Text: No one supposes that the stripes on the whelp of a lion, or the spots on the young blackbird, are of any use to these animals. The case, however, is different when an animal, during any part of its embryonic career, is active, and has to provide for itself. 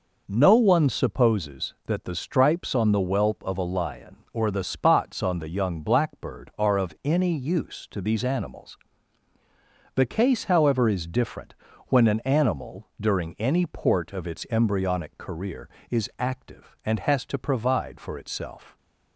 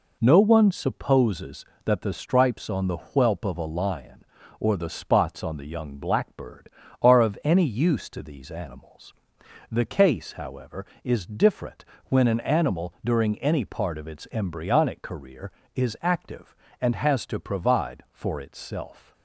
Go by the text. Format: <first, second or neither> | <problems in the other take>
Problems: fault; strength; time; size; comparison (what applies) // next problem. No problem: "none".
second | pauses between "different" and "when"; slight; at 11.5 s; 0.34 s long; slight in the second // says "port" for "part"; at 13.6 s